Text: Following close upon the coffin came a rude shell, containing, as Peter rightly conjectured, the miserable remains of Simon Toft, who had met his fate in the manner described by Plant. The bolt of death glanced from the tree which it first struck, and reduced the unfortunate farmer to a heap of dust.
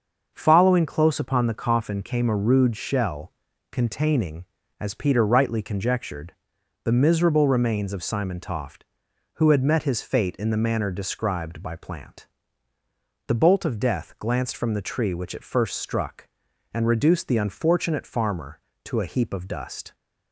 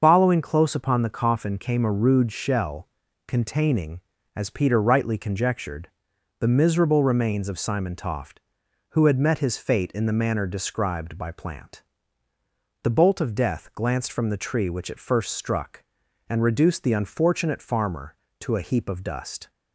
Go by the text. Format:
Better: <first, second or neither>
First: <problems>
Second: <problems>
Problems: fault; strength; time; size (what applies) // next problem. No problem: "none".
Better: first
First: starts louder than the rest; until 1.3 s; 6.5 dB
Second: loses the start of "Following"; at 0.0 s; 125 ms // starts louder than the rest; until 1.0 s; 6.5 dB